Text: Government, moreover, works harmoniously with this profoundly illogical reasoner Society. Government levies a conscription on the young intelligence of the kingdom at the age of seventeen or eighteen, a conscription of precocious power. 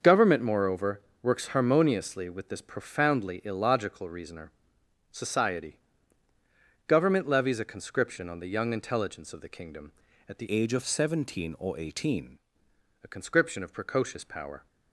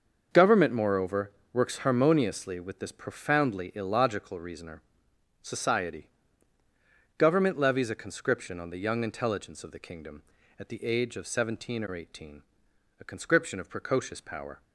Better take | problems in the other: second | starts louder than the rest; until 1.2 s; 6.5 dB; also in the second // pauses between "reasoner" and "Society"; noticeable; at 4.4 s; 0.62 s long; noticeable in the second // changes voice from "age" to "eighteen"; from 10.5 to 12.3 s; 1.8 s long

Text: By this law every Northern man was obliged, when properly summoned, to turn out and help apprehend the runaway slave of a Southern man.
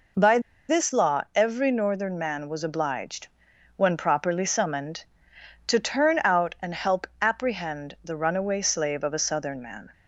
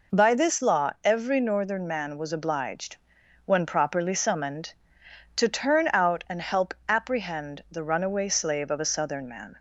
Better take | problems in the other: second | pauses between "By" and "this"; slight; at 0.3 s; 0.29 s long

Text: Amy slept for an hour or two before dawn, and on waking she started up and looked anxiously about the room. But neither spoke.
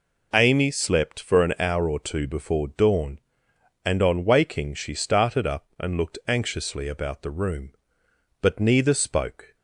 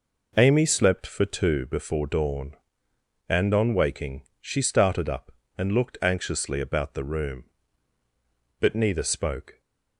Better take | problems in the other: first | skips "an hour or"; at 1.2 s // pauses between "waking" and "she"; slight; at 4.2 s; 0.18 s long

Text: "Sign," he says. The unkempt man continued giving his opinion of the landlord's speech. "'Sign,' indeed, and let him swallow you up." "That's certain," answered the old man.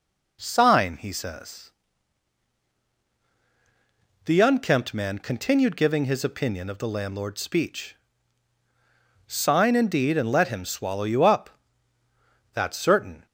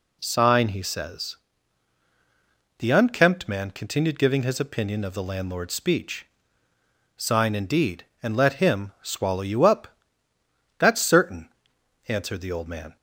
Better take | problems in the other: second | stops before "answered the old man"; at 13.2 s

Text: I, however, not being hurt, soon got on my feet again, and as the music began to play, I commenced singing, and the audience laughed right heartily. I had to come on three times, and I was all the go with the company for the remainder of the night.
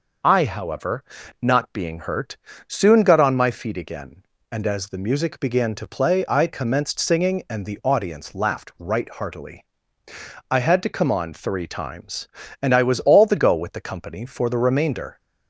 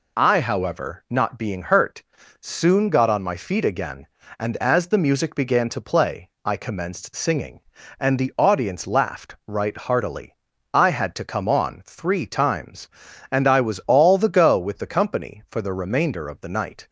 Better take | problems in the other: second | stops before "of the night"; at 15.1 s

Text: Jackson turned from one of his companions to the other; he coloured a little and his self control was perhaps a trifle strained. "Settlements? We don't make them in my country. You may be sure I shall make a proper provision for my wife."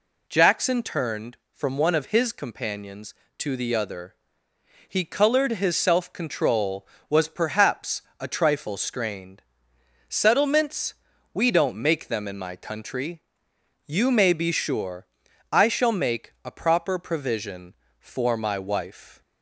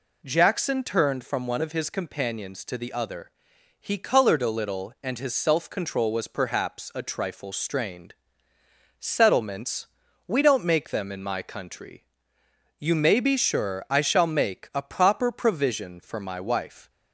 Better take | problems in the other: second | skips "a little and"; at 5.5 s // pauses between "perhaps" and "a"; slight; at 8.0 s; 0.18 s long // pauses between "sure" and "I"; noticeable; at 15.0 s; 0.48 s long

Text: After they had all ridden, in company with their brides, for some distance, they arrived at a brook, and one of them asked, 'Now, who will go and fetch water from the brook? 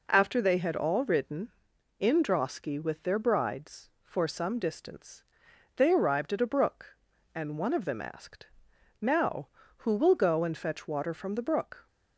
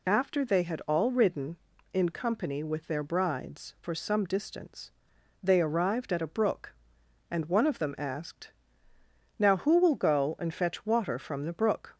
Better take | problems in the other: second | says "drosky" for "company"; at 2.2 s

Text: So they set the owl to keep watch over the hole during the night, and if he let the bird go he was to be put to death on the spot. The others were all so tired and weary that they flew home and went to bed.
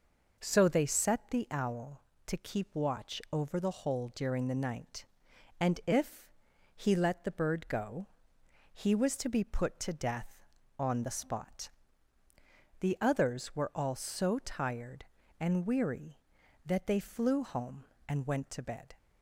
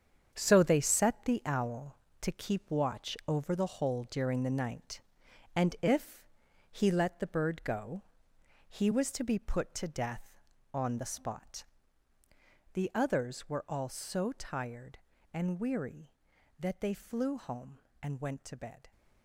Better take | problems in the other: first | gets quieter; strong; throughout; 9.5 dB // pauses between "if" and "he"; noticeable; at 6.2 s; 0.46 s long; noticeable in the first // pauses between "go" and "he"; noticeable; at 8.0 s; 0.66 s long; noticeable in the first

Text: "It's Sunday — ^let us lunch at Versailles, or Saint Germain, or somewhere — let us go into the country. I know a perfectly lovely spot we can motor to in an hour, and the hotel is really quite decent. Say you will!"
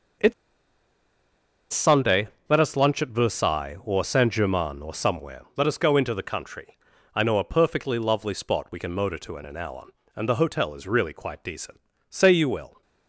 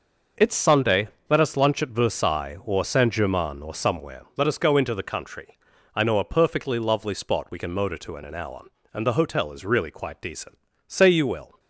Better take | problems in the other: second | pauses between "It's" and "Sunday"; strong; at 0.3 s; 1.3 s long

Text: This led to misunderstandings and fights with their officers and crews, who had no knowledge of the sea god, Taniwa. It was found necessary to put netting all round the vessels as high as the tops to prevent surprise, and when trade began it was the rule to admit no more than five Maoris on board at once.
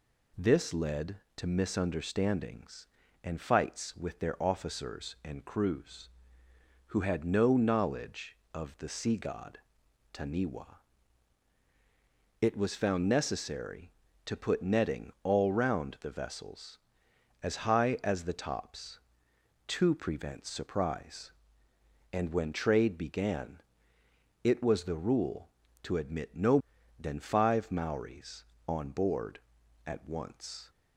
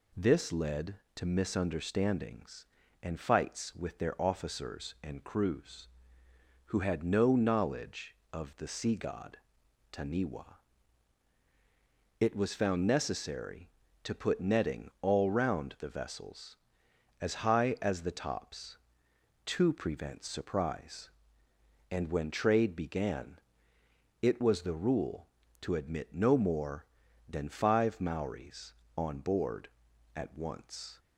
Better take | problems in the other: second | pauses between "began" and "it"; noticeable; at 23.6 s; 0.82 s long; noticeable in the second // skips "more"; at 26.7 s

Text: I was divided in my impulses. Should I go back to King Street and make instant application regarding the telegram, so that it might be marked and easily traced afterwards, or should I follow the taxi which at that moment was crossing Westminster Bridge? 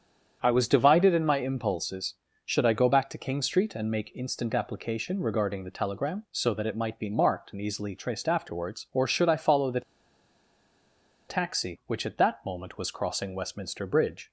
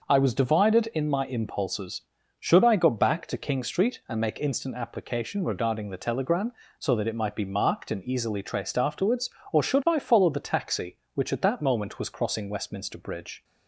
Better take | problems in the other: second | starts louder than the rest; strong; until 1.4 s; 8 dB // pauses between "the" and "taxi"; strong; at 9.8 s; 1.4 s long

